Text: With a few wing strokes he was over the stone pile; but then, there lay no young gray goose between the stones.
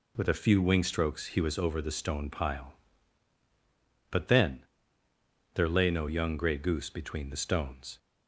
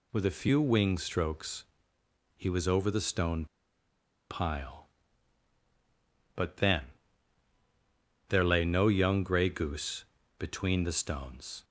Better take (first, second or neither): first